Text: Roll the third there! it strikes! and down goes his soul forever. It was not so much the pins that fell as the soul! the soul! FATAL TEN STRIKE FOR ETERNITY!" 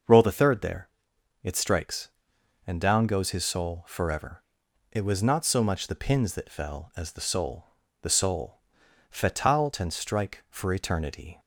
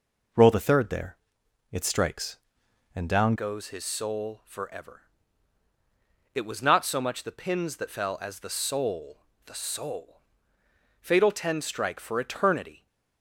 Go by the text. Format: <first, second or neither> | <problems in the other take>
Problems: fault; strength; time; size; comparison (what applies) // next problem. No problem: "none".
first | changes voice at "goes"; from 3.3 s on; 9.5 s long